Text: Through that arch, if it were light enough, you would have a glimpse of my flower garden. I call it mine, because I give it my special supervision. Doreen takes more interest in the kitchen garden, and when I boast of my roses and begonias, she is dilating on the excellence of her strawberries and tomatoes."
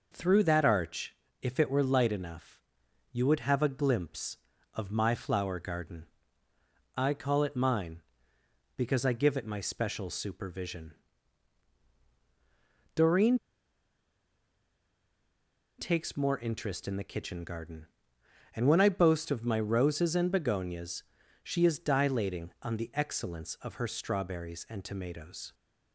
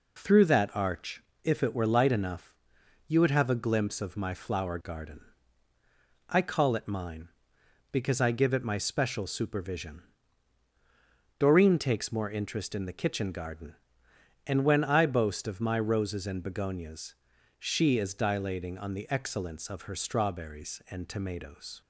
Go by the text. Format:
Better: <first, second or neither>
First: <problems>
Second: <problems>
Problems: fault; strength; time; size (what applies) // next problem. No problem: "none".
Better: second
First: pauses between "Doreen" and "takes"; strong; at 13.3 s; 2.3 s long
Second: none